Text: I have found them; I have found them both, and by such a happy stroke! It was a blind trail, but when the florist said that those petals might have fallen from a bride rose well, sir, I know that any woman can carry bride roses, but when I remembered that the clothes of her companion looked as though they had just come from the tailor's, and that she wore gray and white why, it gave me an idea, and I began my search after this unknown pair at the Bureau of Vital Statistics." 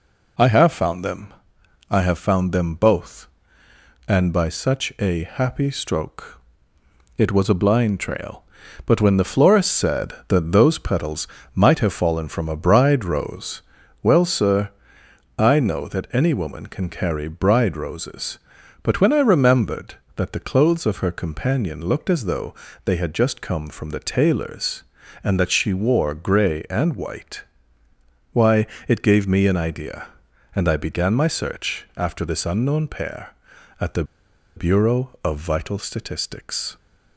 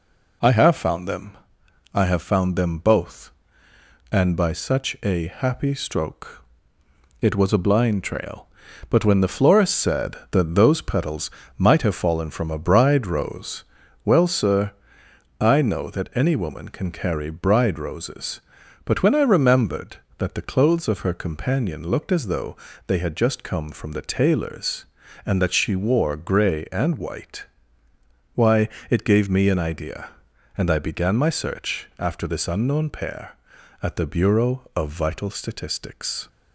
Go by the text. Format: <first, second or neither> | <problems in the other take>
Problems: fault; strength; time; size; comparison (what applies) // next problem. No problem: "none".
second | pauses between "petals" and "might"; slight; at 11.2 s; 0.26 s long; slight in the second // pauses between "rose" and "well"; at 13.5 s; 0.42 s long; also in the second // pauses between "though" and "they"; slight; at 22.5 s; 0.32 s long; slight in the second // pauses between "white" and "why"; noticeable; at 27.4 s; 0.88 s long; noticeable in the second // pauses between "the" and "Bureau"; noticeable; at 34.0 s; 0.52 s long